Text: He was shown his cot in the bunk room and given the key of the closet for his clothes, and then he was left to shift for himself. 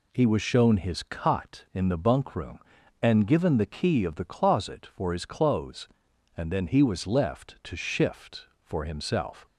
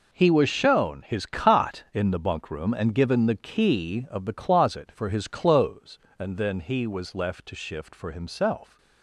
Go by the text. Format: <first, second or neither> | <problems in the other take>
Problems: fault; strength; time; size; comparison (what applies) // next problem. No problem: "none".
neither | none